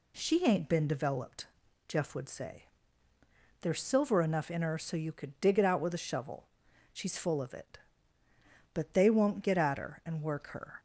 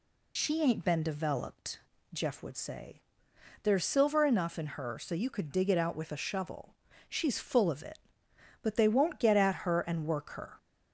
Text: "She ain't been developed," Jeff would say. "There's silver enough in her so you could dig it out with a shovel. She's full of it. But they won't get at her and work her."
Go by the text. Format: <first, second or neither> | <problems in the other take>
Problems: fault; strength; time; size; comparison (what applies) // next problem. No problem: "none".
first | loses the start of "She"; at 0.3 s; 40 ms